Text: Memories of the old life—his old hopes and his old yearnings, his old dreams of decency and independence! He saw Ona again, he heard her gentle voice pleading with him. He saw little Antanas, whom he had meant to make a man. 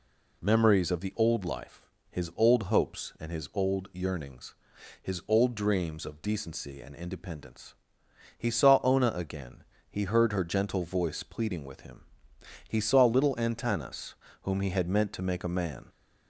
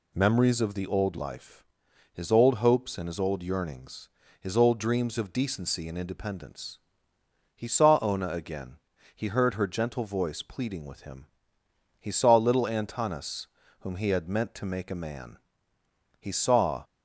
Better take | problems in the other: first | goes on to say "He saw"; noticeable; from 16.1 s on; 0.64 s long

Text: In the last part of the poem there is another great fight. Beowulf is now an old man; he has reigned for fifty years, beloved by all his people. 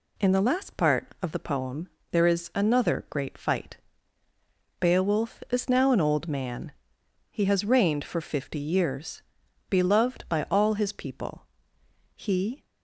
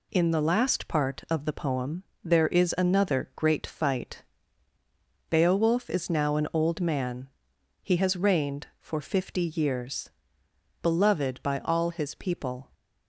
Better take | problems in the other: second | pauses between "poem" and "there"; slight; at 1.8 s; 0.22 s long; slight in the second // goes on to say "He"; from 12.1 s on; 0.50 s long

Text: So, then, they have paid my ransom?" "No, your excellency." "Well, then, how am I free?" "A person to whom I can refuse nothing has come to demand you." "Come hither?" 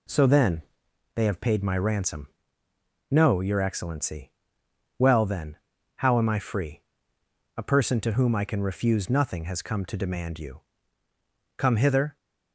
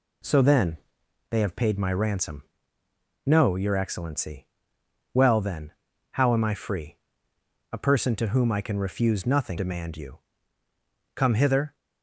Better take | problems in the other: first | skips "has come to"; at 9.5 s

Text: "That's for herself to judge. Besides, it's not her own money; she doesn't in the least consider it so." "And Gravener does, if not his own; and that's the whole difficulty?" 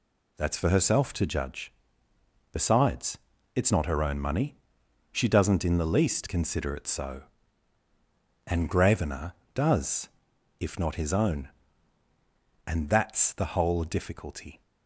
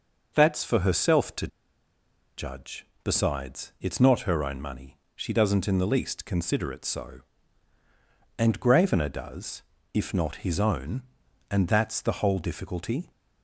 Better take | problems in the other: first | starts louder than the rest; noticeable; until 1.3 s; 6 dB // pauses between "to" and "judge"; noticeable; at 1.4 s; 0.90 s long

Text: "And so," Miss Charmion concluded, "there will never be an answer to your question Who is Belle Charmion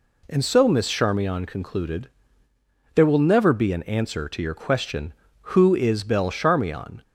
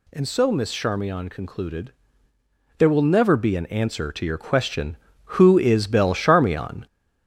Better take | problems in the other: first | gets louder; noticeable; throughout; 5.5 dB

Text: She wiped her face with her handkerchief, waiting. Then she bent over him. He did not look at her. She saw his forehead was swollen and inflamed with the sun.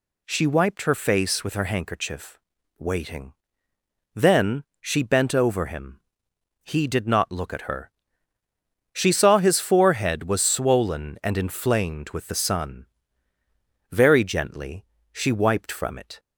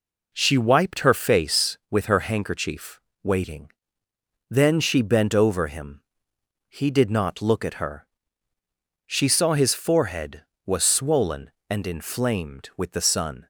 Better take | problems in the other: second | pauses between "Then" and "she"; slight; at 4.6 s; 0.18 s long // goes on to say "Very gently she wiped from it"; strong; from 13.9 s on; 2.2 s long

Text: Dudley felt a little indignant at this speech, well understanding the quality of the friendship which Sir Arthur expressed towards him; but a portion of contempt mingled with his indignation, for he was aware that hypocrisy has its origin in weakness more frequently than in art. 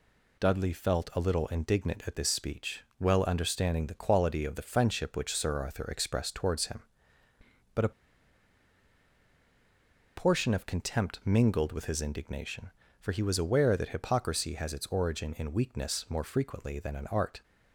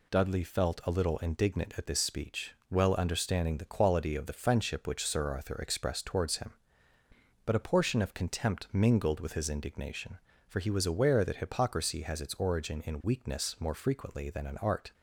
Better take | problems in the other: second | pauses between "a" and "portion"; strong; at 7.9 s; 2.2 s long

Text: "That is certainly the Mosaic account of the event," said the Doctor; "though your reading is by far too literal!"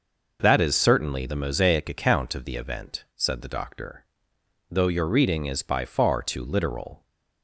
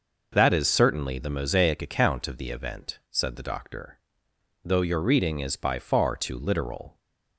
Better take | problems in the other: neither | none

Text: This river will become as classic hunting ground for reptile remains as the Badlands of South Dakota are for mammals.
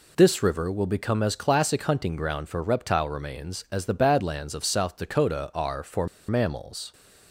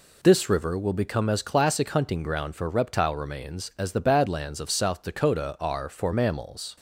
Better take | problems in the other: second | pauses between "for" and "mammals"; slight; at 6.0 s; 0.22 s long

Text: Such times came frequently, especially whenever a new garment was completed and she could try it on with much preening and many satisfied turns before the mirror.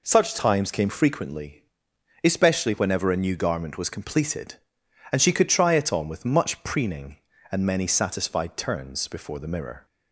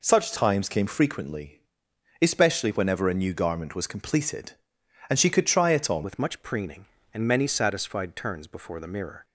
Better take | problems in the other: first | changes voice at "with"; from 6.0 s on; 3.2 s long

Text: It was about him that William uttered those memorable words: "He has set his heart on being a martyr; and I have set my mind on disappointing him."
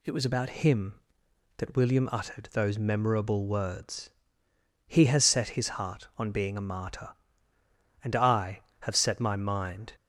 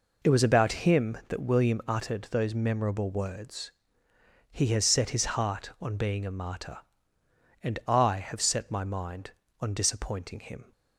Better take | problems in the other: second | stops before "on disappointing him"; at 9.9 s

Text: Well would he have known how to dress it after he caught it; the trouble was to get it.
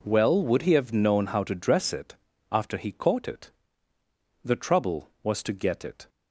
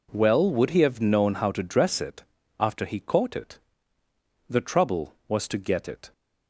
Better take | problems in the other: neither | pauses between "it" and "after"; slight; the same in both

